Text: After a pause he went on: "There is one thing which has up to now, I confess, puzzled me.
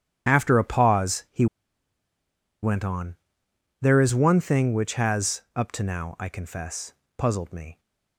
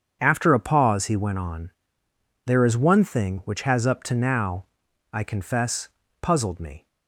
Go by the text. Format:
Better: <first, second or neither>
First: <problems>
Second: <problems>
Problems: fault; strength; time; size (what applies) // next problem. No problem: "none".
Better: second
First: starts louder than the rest; strong; until 1.3 s; 10.5 dB // pauses between "he" and "went"; at 1.4 s; 1.1 s long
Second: starts louder than the rest; strong; until 1.2 s; 7.5 dB